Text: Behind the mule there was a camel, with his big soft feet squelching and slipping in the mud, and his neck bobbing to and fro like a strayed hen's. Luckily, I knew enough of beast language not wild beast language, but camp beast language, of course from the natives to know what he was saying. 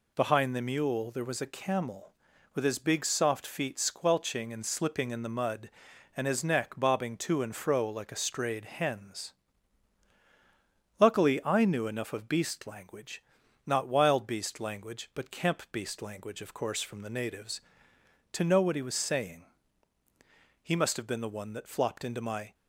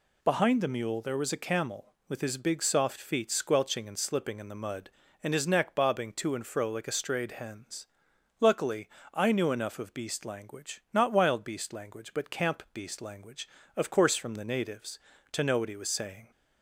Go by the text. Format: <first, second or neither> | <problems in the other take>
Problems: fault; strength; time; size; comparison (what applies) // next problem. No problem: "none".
second | pauses between "language" and "not"; at 13.2 s; 0.44 s long // goes on to say "He must have been the one that flopped into my"; strong; from 20.6 s on; 1.9 s long